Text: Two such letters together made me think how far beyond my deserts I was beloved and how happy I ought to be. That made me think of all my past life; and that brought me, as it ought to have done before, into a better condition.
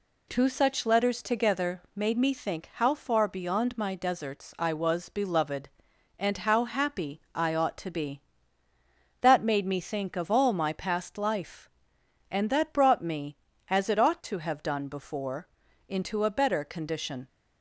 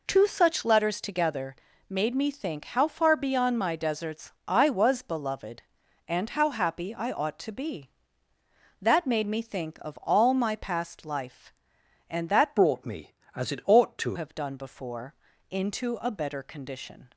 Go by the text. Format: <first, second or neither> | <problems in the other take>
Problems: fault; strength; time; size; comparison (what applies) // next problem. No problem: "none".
first | pauses between "together" and "made"; slight; at 1.5 s; 0.36 s long // pauses between "deserts" and "I"; slight; at 4.3 s; 0.16 s long // changes voice from "brought" to "to"; from 12.5 to 14.1 s; 1.6 s long